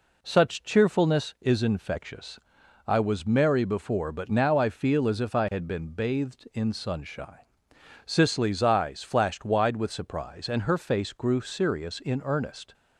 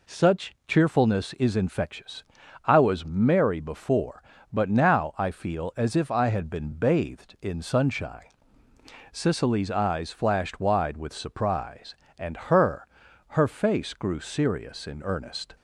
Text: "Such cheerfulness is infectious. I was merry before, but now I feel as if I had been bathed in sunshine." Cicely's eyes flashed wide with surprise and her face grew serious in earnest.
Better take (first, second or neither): first